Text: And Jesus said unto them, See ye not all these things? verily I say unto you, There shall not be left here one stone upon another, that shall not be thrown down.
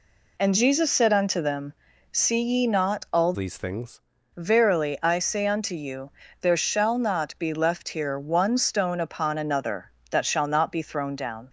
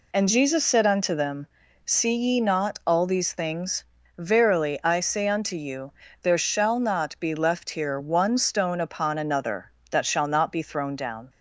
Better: second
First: changes voice from "these" to "things"; from 3.3 to 3.9 s; 0.6 s long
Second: none

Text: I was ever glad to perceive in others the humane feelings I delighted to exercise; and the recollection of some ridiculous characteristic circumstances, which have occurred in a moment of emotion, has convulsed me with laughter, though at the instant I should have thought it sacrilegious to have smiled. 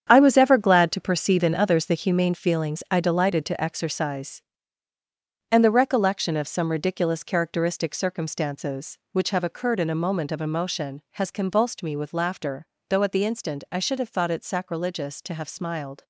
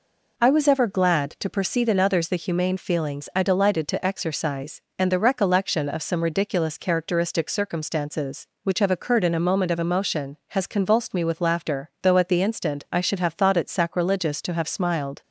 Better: second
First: gets quieter; strong; throughout; 10.5 dB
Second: none

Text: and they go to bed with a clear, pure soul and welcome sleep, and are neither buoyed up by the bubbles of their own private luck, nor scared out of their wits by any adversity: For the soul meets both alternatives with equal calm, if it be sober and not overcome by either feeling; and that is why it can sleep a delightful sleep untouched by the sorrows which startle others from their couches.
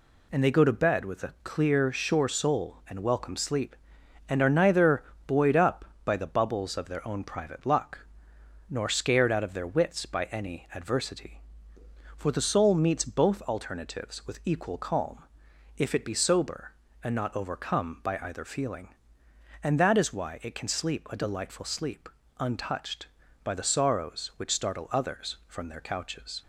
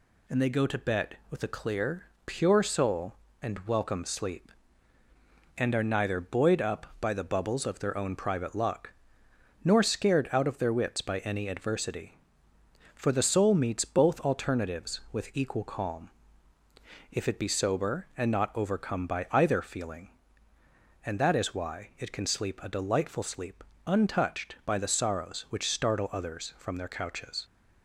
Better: second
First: says "sure" for "pure"; at 1.9 s // pauses between "neither" and "buoyed"; slight; at 5.0 s; 0.22 s long // pauses between "sleep" and "untouched"; slight; at 22.0 s; 0.30 s long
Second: pauses between "sleep" and "untouched"; slight; at 23.6 s; 0.22 s long

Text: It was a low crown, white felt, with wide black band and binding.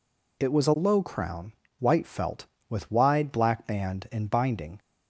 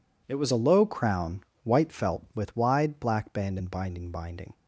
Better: first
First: none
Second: says "binding" twice; at 4.1 s

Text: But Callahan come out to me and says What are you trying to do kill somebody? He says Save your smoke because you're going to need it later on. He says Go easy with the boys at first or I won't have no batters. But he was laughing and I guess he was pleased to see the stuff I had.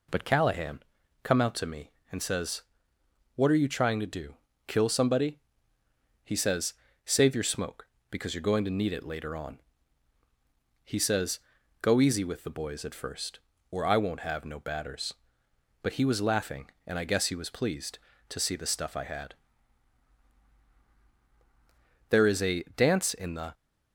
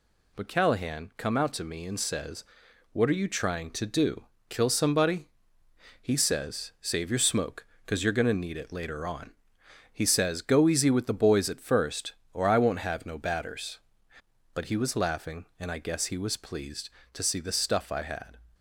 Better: second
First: pauses between "Callahan" and "come"; at 0.7 s; 0.44 s long // pauses between "says" and "What"; noticeable; at 2.6 s; 0.74 s long // pauses between "do" and "kill"; slight; at 4.3 s; 0.32 s long // pauses between "says" and "Save"; slight; at 6.7 s; 0.32 s long // pauses between "says" and "Go"; at 11.3 s; 0.42 s long // goes on to say "There is a dance in the"; from 22.0 s on; 1.4 s long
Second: pauses between "says" and "What"; noticeable; at 2.4 s; 0.50 s long // pauses between "do" and "kill"; slight; at 4.2 s; 0.26 s long

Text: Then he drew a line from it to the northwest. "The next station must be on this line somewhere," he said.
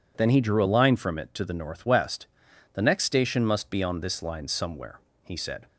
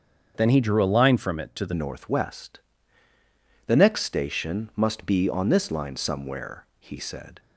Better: first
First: none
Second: starts louder than the rest; strong; until 1.3 s; 7.5 dB // changes voice at "northwest"; from 1.7 s on; 5.6 s long

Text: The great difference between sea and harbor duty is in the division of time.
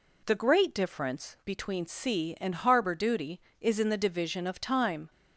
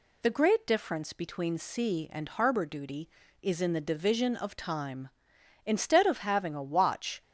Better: first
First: none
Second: goes on to say "Instead of having a watch"; from 5.6 s on; 1.5 s long

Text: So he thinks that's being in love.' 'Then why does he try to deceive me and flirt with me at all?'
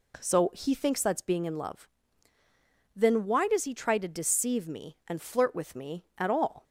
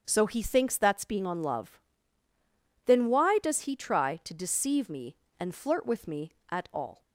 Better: first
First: none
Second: starts louder than the rest; strong; until 1.0 s; 7 dB // says "on" for "in"; at 1.2 s

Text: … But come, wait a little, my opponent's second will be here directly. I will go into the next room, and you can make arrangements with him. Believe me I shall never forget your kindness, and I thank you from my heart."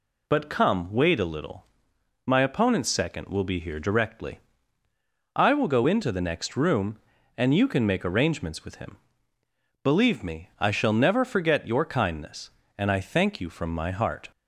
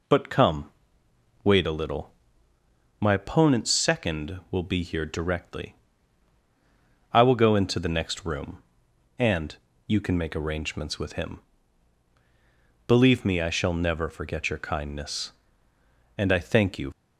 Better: first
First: none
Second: pauses between "and" and "you"; slight; at 9.5 s; 0.30 s long // stops before "from my heart"; at 16.9 s

